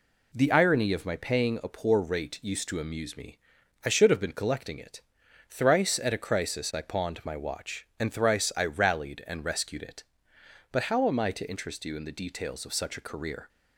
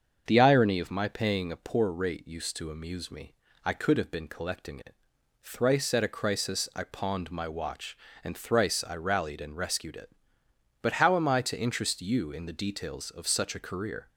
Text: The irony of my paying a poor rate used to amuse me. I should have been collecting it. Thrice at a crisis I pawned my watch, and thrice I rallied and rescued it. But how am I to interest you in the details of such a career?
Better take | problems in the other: first | starts louder than the rest; until 1.2 s; 7 dB // says "could" for "should"; at 3.7 s

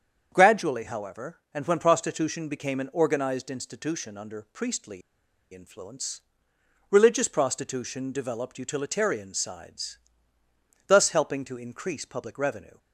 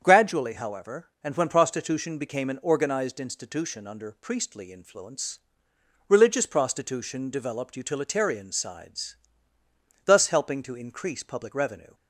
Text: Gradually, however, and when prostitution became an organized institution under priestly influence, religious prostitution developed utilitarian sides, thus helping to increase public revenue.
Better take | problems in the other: second | starts louder than the rest; strong; until 1.3 s; 7.5 dB; strong in the second // pauses between "priestly" and "influence"; noticeable; at 5.0 s; 0.52 s long

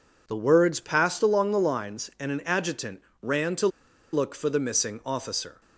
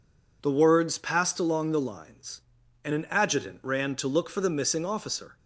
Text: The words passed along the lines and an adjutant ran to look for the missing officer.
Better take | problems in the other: second | pauses between "adjutant" and "ran"; slight; at 3.0 s; 0.20 s long // pauses between "to" and "look"; at 3.6 s; 0.44 s long

